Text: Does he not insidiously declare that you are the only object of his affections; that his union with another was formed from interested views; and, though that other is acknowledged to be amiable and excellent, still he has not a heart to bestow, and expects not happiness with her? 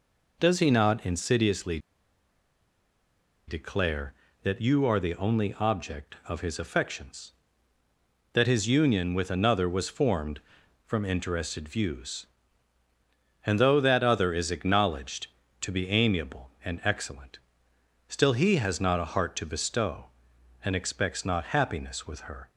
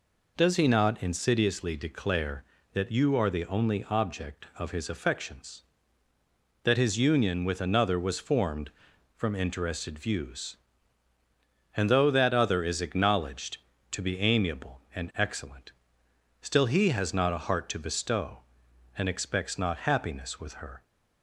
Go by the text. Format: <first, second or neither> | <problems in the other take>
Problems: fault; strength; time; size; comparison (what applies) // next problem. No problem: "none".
second | pauses between "insidiously" and "declare"; strong; at 1.7 s; 1.6 s long